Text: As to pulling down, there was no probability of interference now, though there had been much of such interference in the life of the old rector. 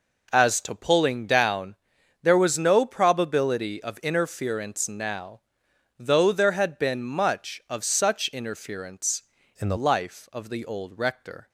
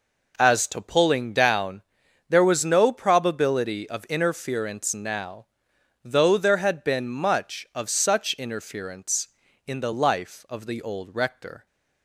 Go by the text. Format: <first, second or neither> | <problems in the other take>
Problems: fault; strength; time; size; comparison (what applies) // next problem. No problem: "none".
second | changes voice from "in" to "the"; from 9.5 to 9.7 s; 0.2 s long